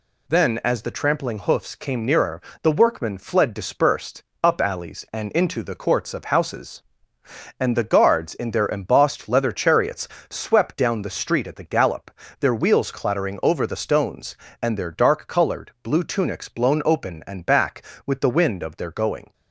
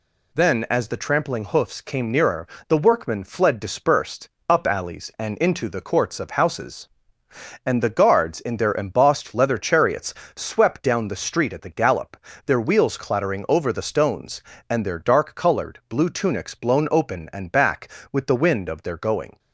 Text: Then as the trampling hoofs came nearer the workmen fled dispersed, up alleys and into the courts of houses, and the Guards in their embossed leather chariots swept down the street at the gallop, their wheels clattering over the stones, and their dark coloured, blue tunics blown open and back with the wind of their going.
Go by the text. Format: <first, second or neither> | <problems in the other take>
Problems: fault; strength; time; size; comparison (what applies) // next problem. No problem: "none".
neither | pauses between "nearer" and "the"; slight; the same in both // pauses between "chariots" and "swept"; slight; the same in both